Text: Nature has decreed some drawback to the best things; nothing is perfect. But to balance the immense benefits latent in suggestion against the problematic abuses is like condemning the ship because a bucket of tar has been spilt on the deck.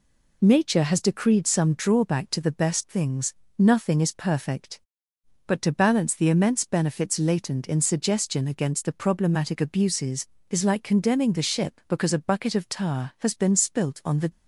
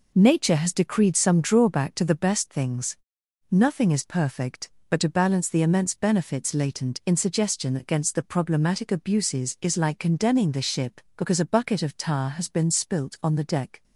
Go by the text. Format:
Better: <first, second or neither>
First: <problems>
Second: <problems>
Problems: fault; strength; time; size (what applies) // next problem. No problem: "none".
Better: second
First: stops before "deck"; at 14.3 s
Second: none